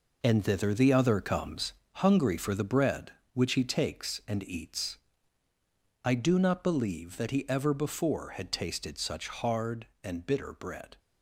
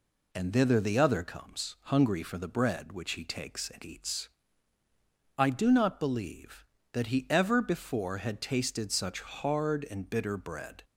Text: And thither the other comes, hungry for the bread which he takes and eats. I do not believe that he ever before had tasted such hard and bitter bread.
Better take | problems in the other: second | gets quieter; strong; throughout; 8.5 dB

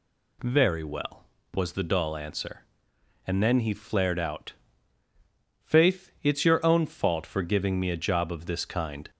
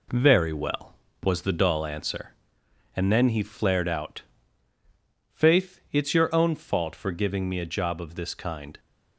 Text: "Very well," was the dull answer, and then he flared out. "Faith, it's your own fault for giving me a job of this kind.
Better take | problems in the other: first | gets quieter; noticeable; throughout; 5 dB

